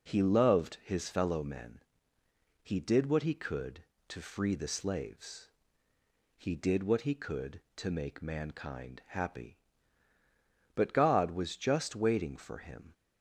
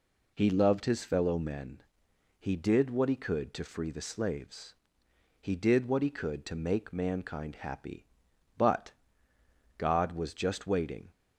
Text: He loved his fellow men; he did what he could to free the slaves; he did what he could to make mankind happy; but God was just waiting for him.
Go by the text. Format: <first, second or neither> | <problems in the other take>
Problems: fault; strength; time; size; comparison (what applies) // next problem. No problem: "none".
first | pauses between "but" and "God"; noticeable; at 8.9 s; 0.86 s long // stops before "for him"; at 11.1 s